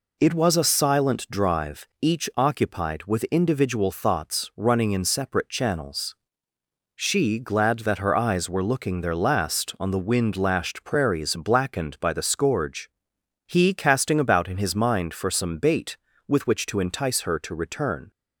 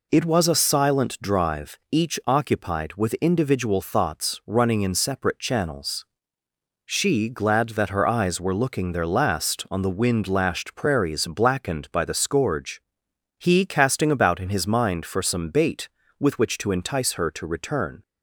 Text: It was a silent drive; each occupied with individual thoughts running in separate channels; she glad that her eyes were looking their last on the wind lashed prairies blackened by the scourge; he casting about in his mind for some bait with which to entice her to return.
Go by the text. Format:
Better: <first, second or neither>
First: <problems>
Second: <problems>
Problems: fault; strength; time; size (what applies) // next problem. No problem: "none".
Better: neither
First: none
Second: none